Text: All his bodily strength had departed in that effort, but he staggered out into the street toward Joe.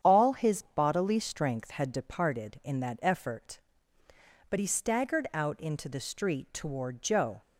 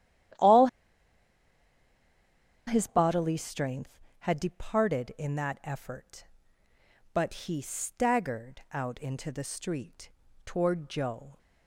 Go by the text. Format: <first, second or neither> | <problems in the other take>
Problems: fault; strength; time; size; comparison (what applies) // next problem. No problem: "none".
first | starts louder than the rest; strong; until 3.3 s; 11.5 dB; strong in the first // pauses between "All" and "his"; strong; at 0.6 s; 2.0 s long // pauses between "street" and "toward"; slight; at 10.0 s; 0.36 s long